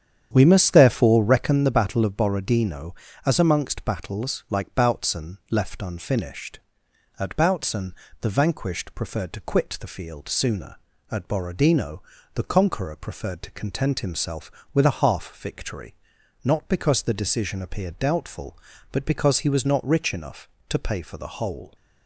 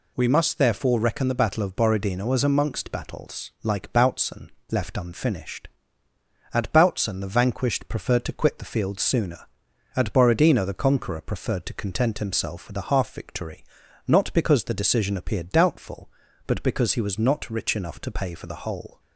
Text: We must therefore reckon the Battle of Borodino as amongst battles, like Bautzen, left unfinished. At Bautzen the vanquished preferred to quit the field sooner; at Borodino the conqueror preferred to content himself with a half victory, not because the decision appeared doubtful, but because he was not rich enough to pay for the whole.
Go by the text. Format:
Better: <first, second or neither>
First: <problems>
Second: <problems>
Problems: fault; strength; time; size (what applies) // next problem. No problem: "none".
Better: second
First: starts louder than the rest; strong; until 1.6 s; 9 dB // pauses between "Bautzen" and "the"; slight; at 7.9 s; 0.26 s long // pauses between "Borodino" and "the"; slight; at 12.0 s; 0.32 s long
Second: none